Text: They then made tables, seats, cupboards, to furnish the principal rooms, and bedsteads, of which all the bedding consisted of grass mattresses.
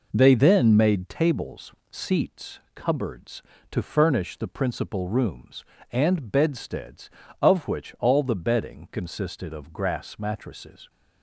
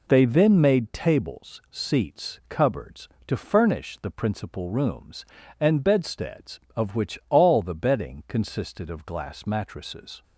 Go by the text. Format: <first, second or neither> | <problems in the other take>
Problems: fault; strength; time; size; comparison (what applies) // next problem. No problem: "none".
first | says "glass" for "grass"; at 9.0 s